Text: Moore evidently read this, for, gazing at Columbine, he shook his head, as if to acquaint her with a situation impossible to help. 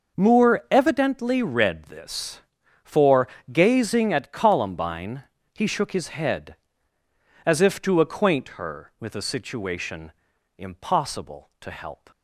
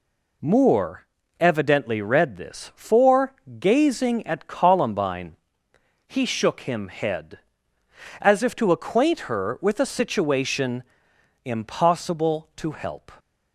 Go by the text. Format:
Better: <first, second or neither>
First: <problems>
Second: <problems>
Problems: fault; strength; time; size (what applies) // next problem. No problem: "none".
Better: first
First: pauses between "situation" and "impossible"; at 10.1 s; 0.44 s long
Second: pauses between "Moore" and "evidently"; slight; at 1.0 s; 0.32 s long // says "him" for "his"; at 6.6 s // pauses between "situation" and "impossible"; noticeable; at 10.8 s; 0.60 s long